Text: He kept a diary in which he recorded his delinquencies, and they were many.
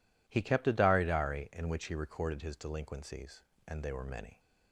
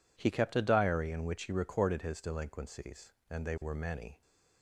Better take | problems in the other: second | says "diary" twice; at 1.0 s

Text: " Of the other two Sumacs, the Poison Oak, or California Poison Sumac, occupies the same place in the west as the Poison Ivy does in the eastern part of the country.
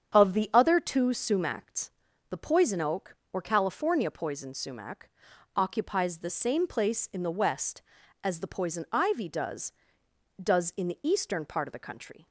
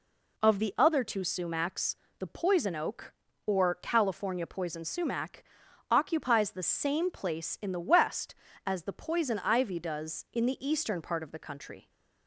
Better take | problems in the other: second | starts louder than the rest; strong; until 1.2 s; 8 dB // says "does" twice; at 10.4 s

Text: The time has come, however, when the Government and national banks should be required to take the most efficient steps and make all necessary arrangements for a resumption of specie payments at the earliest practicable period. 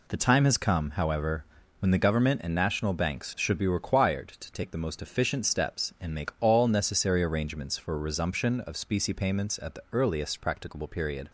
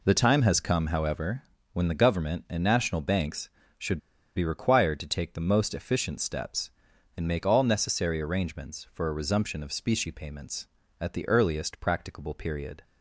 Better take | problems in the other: first | pauses between "should" and "be"; at 3.9 s; 0.36 s long

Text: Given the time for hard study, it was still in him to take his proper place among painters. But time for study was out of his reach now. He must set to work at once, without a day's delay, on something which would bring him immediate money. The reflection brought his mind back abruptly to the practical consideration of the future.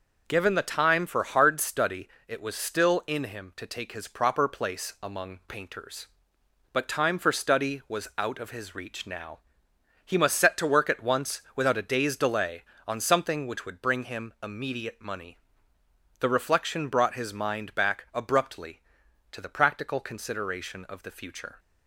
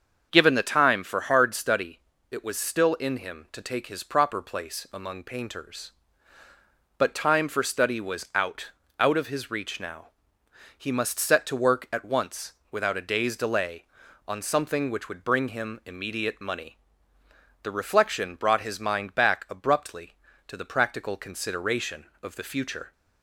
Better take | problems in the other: first | starts louder than the rest; until 1.3 s; 7 dB // says "out" twice; at 8.9 s

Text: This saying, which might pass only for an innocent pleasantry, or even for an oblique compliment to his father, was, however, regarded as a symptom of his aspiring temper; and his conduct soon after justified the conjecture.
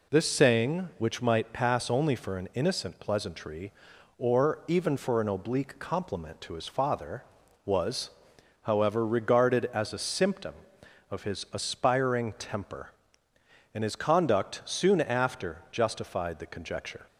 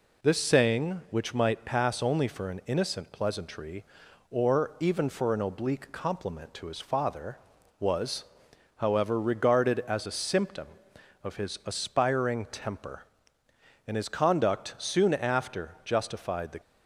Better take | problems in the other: first | stops before "conjecture"; at 16.6 s

